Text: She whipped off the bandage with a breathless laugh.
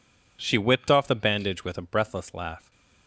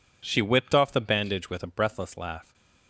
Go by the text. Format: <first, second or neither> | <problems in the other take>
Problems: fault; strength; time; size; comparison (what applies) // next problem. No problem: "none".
neither | none